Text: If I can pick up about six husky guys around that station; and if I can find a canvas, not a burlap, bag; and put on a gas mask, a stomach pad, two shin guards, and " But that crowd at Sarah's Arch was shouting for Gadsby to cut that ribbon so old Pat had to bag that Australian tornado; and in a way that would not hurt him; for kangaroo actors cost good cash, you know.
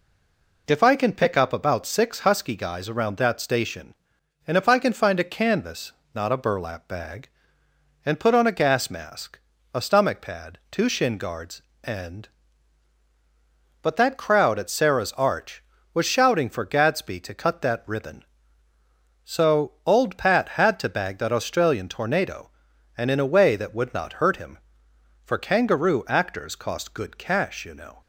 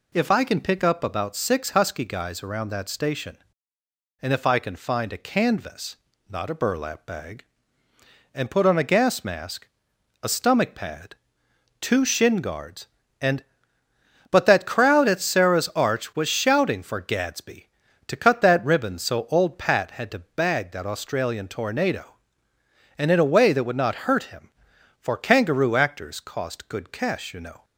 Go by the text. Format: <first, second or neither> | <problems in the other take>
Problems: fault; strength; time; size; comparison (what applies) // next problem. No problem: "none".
second | stays silent before the first word; slight; until 0.6 s; 0.6 s long // pauses between "so" and "old"; slight; at 19.7 s; 0.16 s long